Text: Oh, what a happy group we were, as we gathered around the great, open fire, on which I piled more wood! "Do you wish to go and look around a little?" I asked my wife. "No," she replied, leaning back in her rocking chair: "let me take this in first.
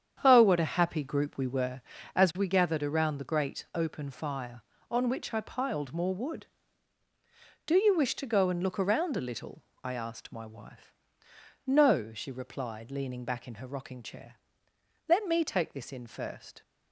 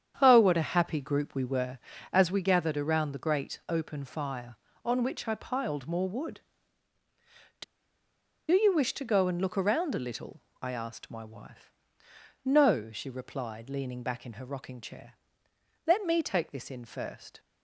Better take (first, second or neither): first